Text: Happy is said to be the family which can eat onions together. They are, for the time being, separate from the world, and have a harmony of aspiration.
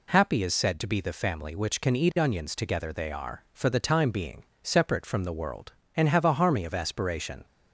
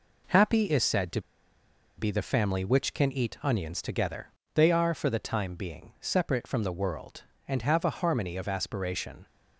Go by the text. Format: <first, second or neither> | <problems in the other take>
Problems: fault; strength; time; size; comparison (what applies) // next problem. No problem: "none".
first | pauses between "to" and "be"; noticeable; at 1.2 s; 0.76 s long